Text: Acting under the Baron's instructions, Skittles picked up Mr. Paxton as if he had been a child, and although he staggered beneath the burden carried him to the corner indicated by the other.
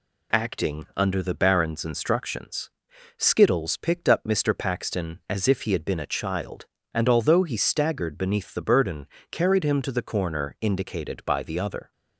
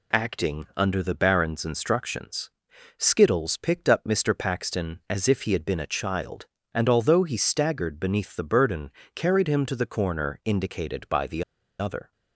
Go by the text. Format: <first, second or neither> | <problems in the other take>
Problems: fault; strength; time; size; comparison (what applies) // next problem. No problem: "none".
first | pauses between "burden" and "carried"; slight; at 8.8 s; 0.26 s long; slight in the first // pauses between "the" and "other"; at 11.4 s; 0.37 s long